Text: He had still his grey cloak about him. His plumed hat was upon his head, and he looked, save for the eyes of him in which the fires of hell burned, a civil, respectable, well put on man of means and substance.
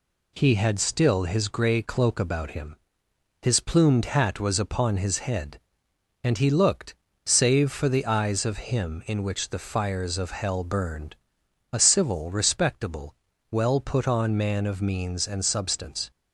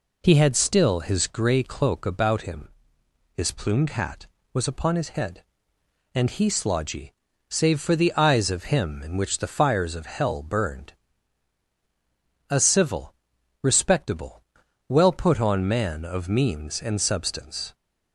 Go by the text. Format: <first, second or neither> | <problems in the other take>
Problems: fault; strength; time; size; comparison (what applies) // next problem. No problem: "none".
first | says "slodgy" for "looked"; at 6.4 s